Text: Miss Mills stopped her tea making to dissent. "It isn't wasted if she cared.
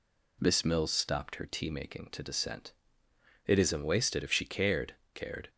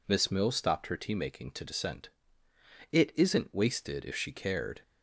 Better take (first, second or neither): second